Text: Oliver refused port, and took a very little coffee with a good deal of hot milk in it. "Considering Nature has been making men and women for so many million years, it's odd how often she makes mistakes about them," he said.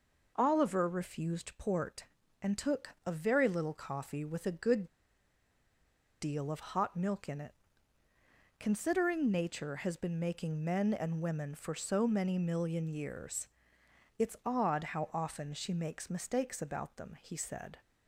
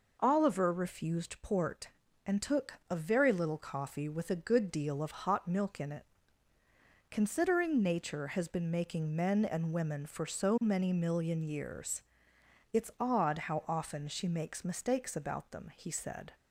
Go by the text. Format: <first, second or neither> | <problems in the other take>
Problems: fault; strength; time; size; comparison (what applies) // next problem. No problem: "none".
second | pauses between "took" and "a"; slight; at 2.8 s; 0.16 s long; slight in the second // pauses between "good" and "deal"; strong; at 4.8 s; 1.3 s long